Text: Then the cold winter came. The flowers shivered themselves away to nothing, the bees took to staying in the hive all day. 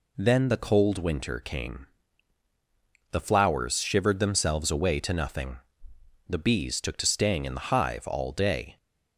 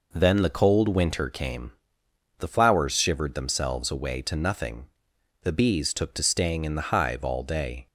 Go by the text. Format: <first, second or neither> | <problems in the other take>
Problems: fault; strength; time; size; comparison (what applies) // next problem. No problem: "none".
neither | none